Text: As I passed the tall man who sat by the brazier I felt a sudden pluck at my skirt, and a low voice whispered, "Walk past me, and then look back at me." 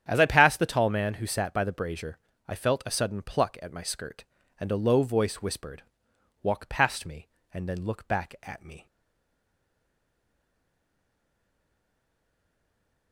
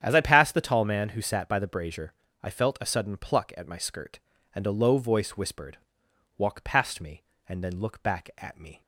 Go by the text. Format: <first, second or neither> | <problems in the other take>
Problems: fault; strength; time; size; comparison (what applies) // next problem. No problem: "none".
second | starts louder than the rest; strong; until 1.0 s; 9 dB; strong in the second // pauses between "brazier" and "I"; slight; at 2.1 s; 0.30 s long; slight in the second // stays silent after the last word; strong; from 8.8 s on; 4.3 s long